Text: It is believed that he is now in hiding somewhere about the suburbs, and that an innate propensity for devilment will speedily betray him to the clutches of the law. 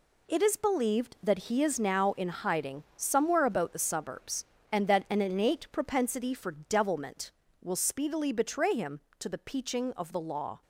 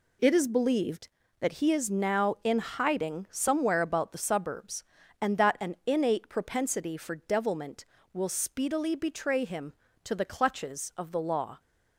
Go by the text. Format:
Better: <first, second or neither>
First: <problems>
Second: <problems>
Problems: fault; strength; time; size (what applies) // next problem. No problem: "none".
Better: second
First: says "peaching" for "clutches"; at 9.3 s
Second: none